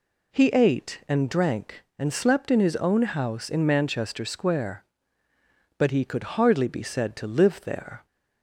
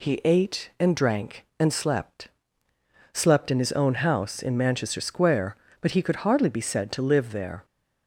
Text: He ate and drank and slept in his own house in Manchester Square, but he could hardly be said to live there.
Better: first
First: none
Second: says "slept" twice; at 3.1 s

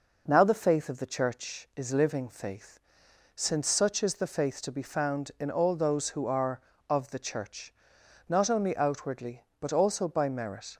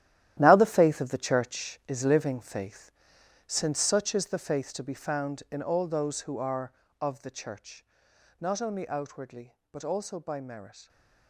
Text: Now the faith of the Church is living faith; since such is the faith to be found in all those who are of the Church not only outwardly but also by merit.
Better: first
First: pauses between "Church" and "not"; noticeable; at 7.7 s; 0.56 s long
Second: gets quieter; strong; throughout; 11.5 dB // pauses between "Church" and "not"; noticeable; at 7.8 s; 0.56 s long

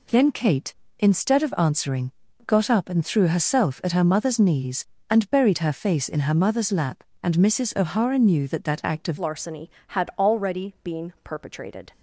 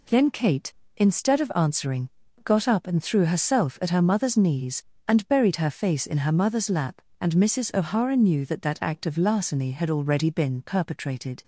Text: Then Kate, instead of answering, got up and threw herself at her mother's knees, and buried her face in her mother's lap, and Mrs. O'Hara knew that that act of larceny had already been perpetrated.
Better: second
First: changes voice at "larceny"; from 9.1 s on; 2.8 s long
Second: none

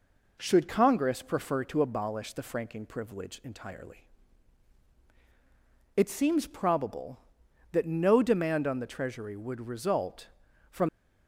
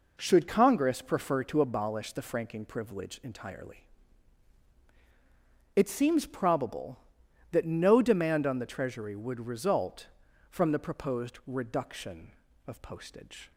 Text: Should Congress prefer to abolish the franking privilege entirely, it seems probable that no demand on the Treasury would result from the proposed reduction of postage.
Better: second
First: stops before "the proposed reduction of postage"; at 10.8 s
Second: none

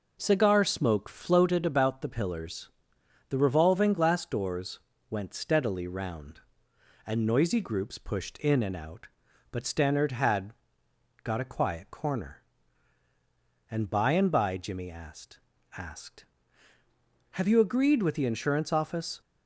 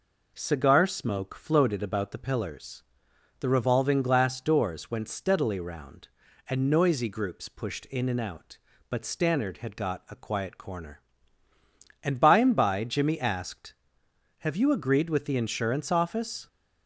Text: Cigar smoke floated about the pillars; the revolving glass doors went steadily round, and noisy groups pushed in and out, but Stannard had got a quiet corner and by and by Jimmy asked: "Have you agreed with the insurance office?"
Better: second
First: pauses between "doors" and "went"; slight; at 4.8 s; 0.30 s long // pauses between "had" and "got"; noticeable; at 10.5 s; 0.68 s long // says "asked" twice; at 15.7 s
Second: none

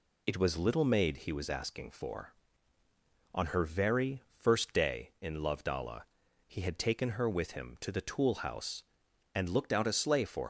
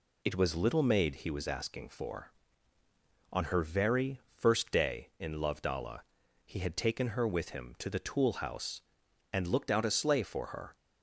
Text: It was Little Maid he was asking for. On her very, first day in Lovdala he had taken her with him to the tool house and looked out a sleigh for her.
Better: second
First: pauses between "Lovdala" and "he"; at 6.0 s; 0.44 s long // stops before "her"; at 10.4 s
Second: pauses between "Lovdala" and "he"; at 5.9 s; 0.44 s long

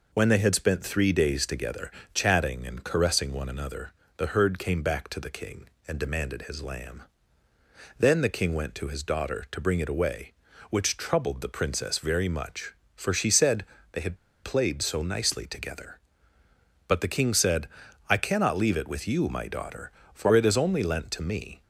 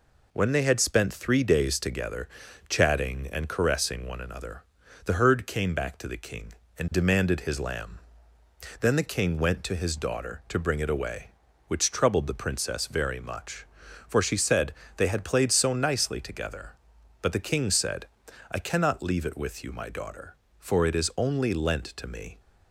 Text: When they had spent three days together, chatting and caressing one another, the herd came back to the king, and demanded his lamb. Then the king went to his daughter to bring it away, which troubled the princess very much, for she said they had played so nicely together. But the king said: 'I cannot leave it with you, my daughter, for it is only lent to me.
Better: second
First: pauses between "said" and "they"; slight; at 13.6 s; 0.26 s long // pauses between "had" and "played"; slight; at 14.1 s; 0.26 s long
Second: pauses between "said" and "they"; slight; at 14.7 s; 0.24 s long

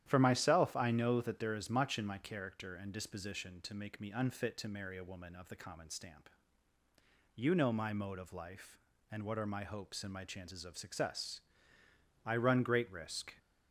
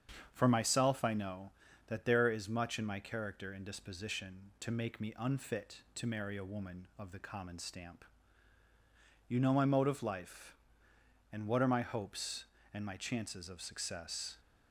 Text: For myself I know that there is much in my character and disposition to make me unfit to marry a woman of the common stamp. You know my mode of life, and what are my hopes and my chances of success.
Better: second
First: starts louder than the rest; strong; until 1.0 s; 11 dB // goes on to say "I run great risk"; noticeable; from 12.2 s on; 1.1 s long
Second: starts louder than the rest; strong; until 1.3 s; 7.5 dB

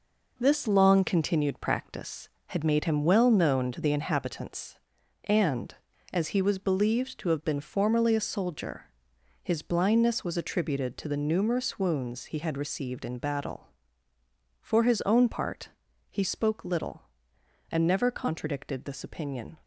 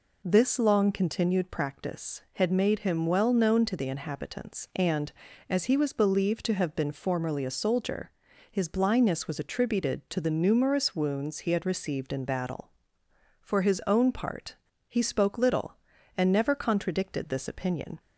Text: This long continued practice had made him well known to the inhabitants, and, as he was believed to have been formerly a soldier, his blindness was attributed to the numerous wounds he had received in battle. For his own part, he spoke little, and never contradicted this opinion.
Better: second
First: gets quieter; throughout; 6.5 dB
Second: none

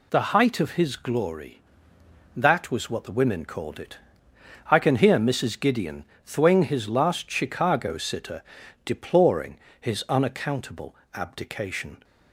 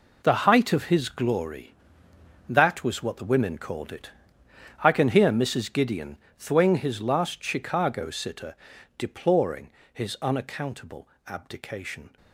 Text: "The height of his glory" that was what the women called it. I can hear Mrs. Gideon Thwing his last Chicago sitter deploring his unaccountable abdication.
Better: first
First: pauses between "Gideon" and "Thwing"; slight; at 6.0 s; 0.24 s long // pauses between "sitter" and "deploring"; at 8.4 s; 0.42 s long // pauses between "deploring" and "his"; slight; at 9.5 s; 0.22 s long // pauses between "unaccountable" and "abdication"; slight; at 10.9 s; 0.22 s long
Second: gets quieter; strong; throughout; 11.5 dB // pauses between "Gideon" and "Thwing"; slight; at 6.1 s; 0.24 s long // pauses between "sitter" and "deploring"; at 8.5 s; 0.42 s long // pauses between "deploring" and "his"; slight; at 9.7 s; 0.22 s long // pauses between "unaccountable" and "abdication"; slight; at 11.0 s; 0.22 s long

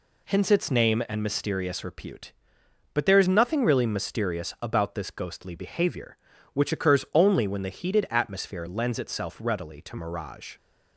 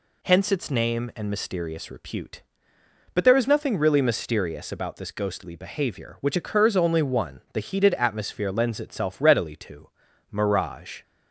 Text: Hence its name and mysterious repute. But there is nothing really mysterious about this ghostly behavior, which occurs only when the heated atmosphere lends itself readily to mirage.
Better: first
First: none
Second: says "one" for "when"; at 7.0 s // pauses between "to" and "mirage"; at 9.8 s; 0.42 s long

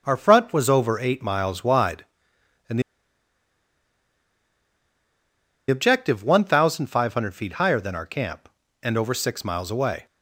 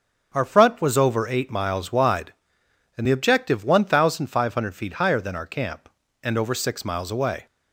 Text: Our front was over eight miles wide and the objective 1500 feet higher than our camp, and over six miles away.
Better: second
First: starts louder than the rest; until 1.0 s; 6.5 dB // pauses between "the" and "objective"; strong; at 2.8 s; 2.8 s long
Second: starts louder than the rest; until 1.3 s; 6.5 dB

